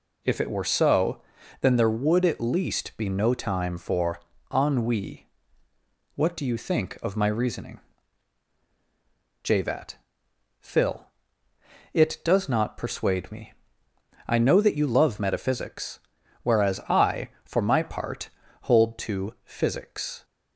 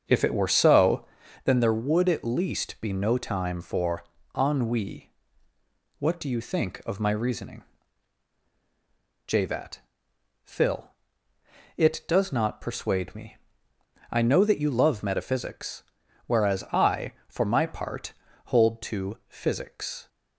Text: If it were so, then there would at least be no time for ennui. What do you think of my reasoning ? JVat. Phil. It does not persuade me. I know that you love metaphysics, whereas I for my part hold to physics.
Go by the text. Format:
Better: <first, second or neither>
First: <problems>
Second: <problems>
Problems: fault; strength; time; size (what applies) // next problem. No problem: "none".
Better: first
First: pauses between "for" and "ennui"; slight; at 4.2 s; 0.32 s long // pauses between "part" and "hold"; slight; at 18.2 s; 0.34 s long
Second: starts louder than the rest; until 1.3 s; 7 dB // pauses between "for" and "ennui"; slight; at 4.0 s; 0.32 s long // pauses between "part" and "hold"; slight; at 18.1 s; 0.34 s long